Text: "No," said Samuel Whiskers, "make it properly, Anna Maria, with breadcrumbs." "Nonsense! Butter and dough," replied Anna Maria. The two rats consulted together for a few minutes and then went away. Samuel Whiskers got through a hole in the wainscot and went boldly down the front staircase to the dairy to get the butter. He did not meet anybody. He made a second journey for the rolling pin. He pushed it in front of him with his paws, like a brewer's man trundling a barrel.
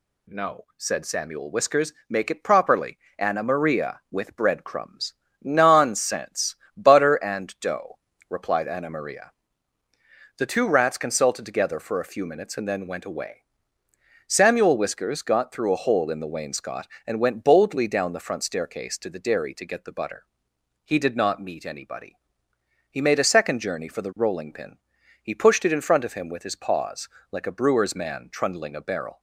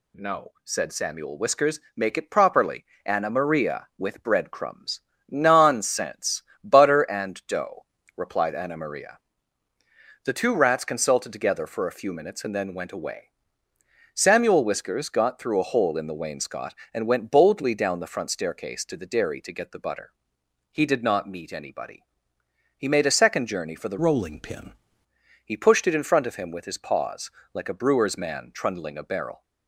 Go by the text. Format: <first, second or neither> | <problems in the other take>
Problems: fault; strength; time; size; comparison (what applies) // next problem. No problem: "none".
first | changes voice from "rolling" to "pin"; from 23.9 to 24.7 s; 0.8 s long